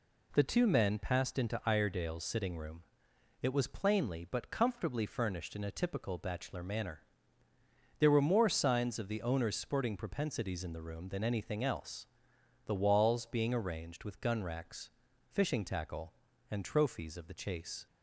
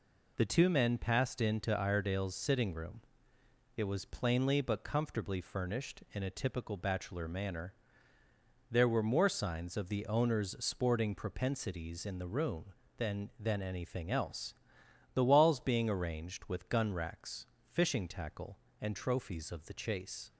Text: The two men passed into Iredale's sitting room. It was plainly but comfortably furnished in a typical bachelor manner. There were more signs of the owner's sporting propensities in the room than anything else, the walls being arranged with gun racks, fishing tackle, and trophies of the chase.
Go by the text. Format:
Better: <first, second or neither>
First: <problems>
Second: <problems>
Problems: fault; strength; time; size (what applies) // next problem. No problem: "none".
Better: first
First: none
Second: says "than" twice; at 13.3 s